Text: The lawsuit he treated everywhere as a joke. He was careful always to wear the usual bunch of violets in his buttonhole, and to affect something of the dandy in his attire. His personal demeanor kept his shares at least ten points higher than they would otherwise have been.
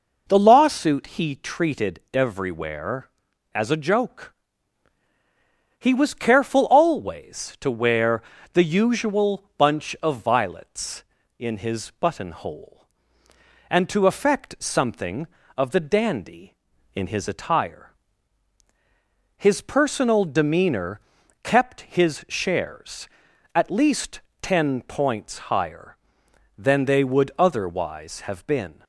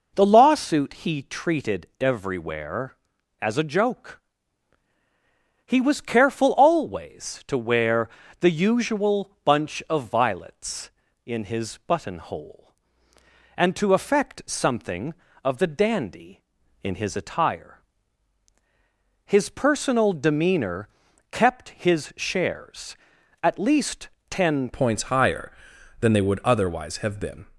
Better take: first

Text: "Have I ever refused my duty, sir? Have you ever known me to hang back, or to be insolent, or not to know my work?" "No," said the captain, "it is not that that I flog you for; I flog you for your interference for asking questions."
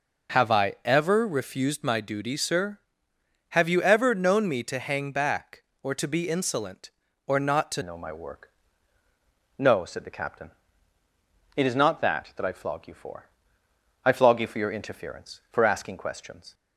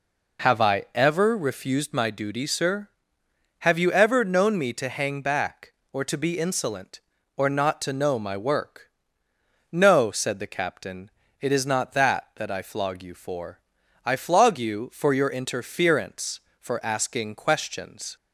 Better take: second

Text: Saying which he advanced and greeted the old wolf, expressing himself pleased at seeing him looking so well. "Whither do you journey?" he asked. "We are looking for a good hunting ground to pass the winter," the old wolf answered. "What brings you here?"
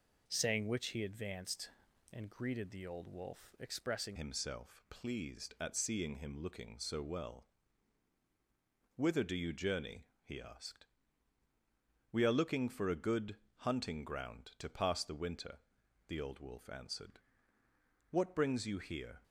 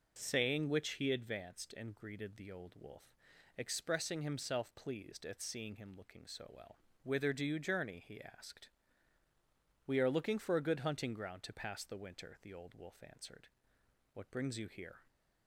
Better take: second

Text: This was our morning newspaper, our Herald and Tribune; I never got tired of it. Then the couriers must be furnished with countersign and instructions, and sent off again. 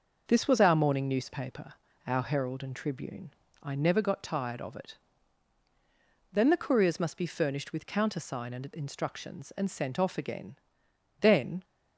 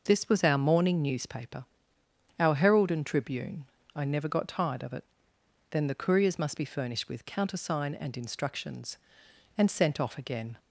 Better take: second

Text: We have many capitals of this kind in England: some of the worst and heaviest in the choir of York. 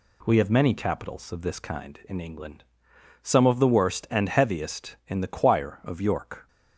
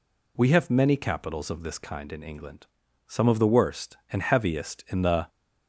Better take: first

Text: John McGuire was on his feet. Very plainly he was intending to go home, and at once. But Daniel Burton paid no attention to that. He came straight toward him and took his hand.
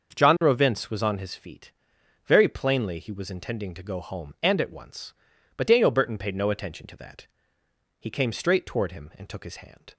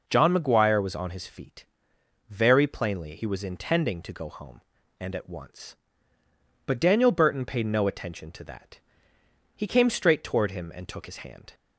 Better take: second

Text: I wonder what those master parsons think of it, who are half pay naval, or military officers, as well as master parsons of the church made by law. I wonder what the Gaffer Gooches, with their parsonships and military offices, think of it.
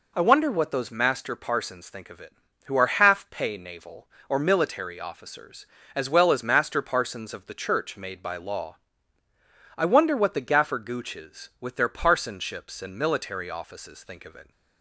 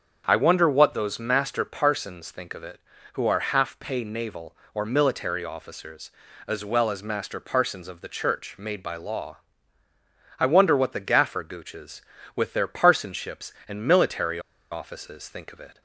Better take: first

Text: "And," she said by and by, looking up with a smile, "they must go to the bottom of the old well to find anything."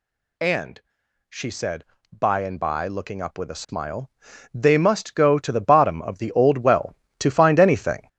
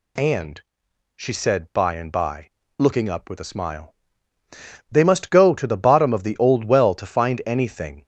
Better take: second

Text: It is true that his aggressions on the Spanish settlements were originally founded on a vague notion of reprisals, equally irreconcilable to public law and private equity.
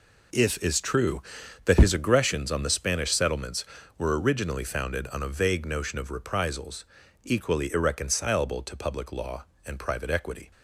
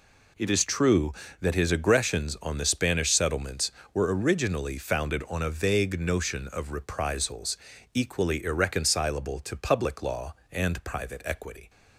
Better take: second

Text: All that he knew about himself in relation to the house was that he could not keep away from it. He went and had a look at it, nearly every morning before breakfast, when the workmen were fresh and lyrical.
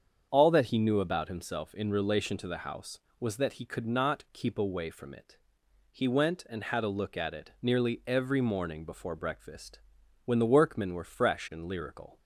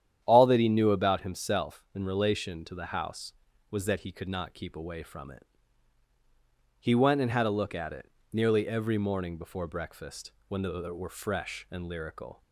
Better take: first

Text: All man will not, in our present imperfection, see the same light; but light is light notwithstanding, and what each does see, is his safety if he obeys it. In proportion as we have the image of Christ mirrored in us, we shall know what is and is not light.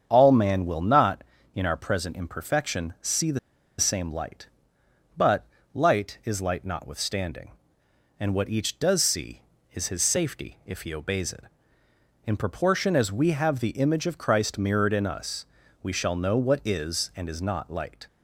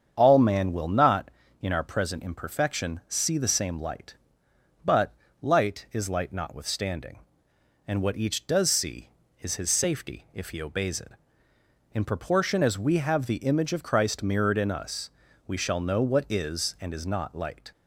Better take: second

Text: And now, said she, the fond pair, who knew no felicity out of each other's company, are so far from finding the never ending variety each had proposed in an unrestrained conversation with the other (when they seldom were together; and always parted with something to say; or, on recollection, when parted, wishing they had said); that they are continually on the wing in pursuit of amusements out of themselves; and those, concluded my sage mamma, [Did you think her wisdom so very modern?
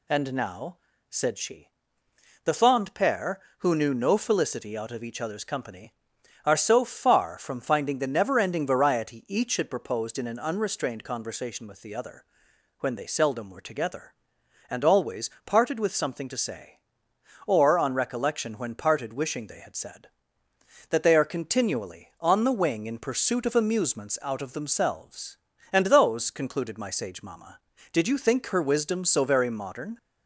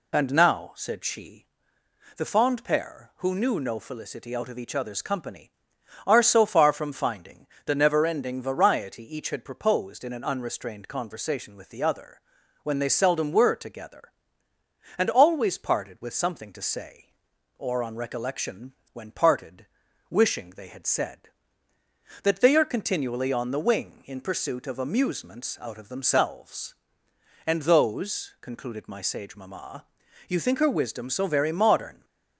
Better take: first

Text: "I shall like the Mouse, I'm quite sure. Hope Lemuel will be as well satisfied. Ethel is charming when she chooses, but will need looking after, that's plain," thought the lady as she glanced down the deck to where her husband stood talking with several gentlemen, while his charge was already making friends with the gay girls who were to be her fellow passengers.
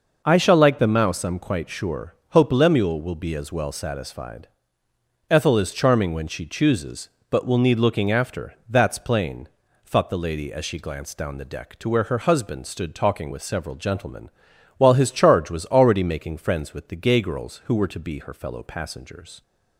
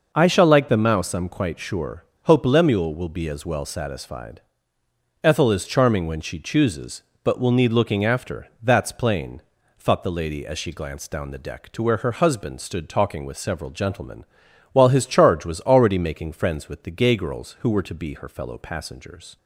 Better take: neither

